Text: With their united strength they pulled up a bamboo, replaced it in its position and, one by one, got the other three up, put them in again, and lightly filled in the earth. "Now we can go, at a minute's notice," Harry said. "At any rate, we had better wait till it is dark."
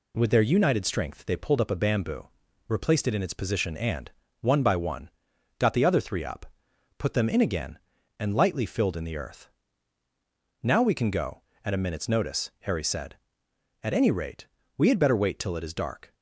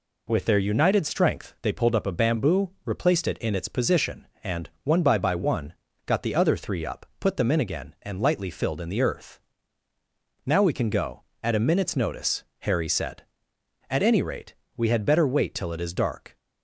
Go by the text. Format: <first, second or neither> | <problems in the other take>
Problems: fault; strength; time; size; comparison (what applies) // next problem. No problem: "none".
first | says "by" twice; at 5.1 s